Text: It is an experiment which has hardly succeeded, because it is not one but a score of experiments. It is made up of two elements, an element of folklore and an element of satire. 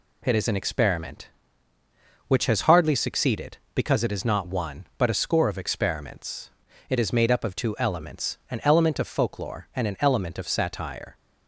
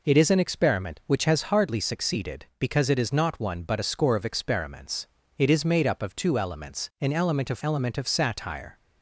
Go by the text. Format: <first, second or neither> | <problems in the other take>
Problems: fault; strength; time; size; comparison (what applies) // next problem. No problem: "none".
first | skips "folklore and an"; at 7.6 s